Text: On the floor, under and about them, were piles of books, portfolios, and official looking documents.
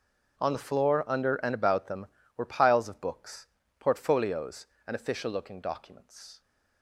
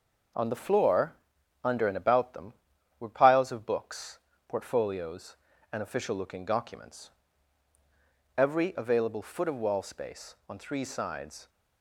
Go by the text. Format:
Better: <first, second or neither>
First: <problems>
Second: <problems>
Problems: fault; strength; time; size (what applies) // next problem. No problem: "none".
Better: first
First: none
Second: goes on to say "Every available foot of wall space on three sides"; strong; from 8.3 s on; 3.1 s long